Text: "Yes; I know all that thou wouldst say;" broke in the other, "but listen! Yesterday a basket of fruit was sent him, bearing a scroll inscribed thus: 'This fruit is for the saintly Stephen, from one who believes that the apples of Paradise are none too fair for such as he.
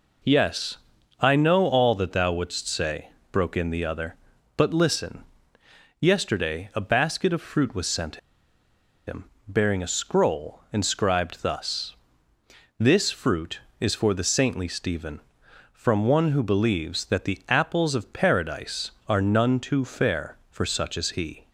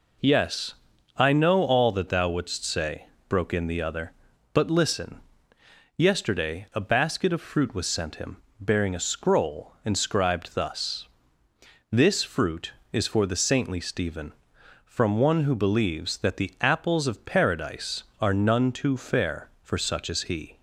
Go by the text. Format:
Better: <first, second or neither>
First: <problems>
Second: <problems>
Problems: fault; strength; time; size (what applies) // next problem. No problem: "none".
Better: second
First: pauses between "sent" and "him"; noticeable; at 8.1 s; 0.90 s long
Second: none